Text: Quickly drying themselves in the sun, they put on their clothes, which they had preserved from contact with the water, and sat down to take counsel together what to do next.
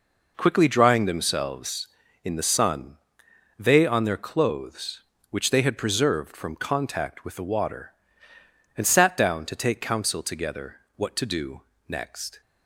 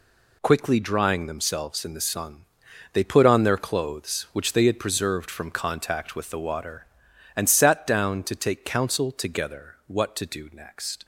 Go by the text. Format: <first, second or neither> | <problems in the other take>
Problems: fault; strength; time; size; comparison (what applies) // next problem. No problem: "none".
second | skips "put"; at 3.8 s // pauses between "together" and "what"; slight; at 10.7 s; 0.20 s long // pauses between "do" and "next"; slight; at 11.6 s; 0.24 s long